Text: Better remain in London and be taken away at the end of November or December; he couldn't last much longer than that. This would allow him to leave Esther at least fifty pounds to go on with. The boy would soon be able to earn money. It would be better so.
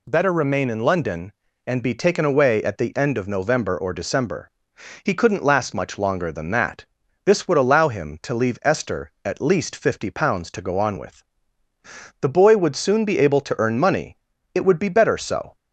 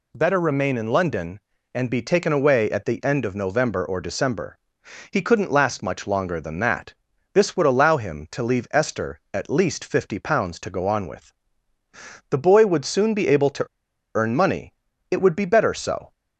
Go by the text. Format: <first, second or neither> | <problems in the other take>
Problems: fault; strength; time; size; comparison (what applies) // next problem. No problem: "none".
first | pauses between "to" and "earn"; noticeable; at 13.6 s; 0.51 s long